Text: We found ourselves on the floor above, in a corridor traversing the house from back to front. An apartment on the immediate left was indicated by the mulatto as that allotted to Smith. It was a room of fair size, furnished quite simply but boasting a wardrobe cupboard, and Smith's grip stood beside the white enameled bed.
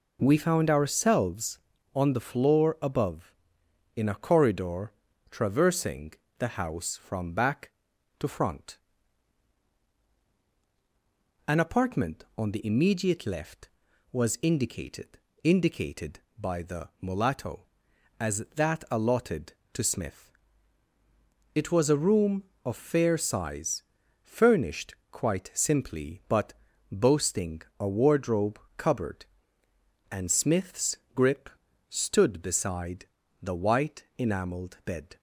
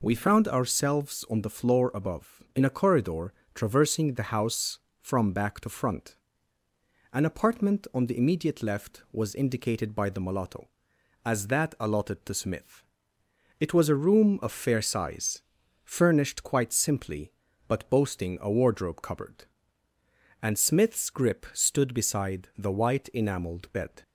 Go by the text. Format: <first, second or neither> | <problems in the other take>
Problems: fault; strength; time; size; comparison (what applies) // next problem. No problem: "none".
second | pauses between "corridor" and "traversing"; at 4.9 s; 0.38 s long; slight in the second // pauses between "traversing" and "the"; slight; at 6.1 s; 0.24 s long // says "indicated" twice; at 15.4 s // pauses between "furnished" and "quite"; slight; at 24.9 s; 0.18 s long // pauses between "but" and "boasting"; at 26.5 s; 0.40 s long // pauses between "boasting" and "a"; slight; at 27.6 s; 0.16 s long // pauses between "wardrobe" and "cupboard"; slight; at 28.5 s; 0.18 s long // pauses between "Smith's" and "grip"; slight; at 30.9 s; 0.18 s long // pauses between "grip" and "stood"; at 31.4 s; 0.40 s long // pauses between "beside" and "the"; slight; at 33.0 s; 0.36 s long // pauses between "white" and "enameled"; slight; at 34.0 s; 0.16 s long